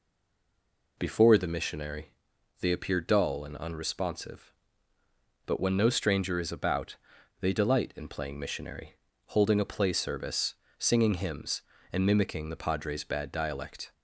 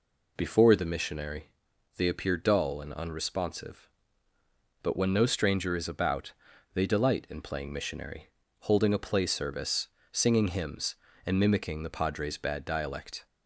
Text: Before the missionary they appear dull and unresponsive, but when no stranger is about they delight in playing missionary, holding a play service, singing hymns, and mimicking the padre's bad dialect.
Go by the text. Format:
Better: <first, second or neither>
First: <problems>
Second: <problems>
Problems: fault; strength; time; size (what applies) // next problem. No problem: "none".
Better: second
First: stays silent before the first word; until 0.9 s; 0.9 s long // pauses between "missionary" and "they"; noticeable; at 2.1 s; 0.48 s long // pauses between "about" and "they"; at 6.9 s; 0.43 s long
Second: pauses between "missionary" and "they"; noticeable; at 1.4 s; 0.46 s long // pauses between "about" and "they"; at 6.3 s; 0.40 s long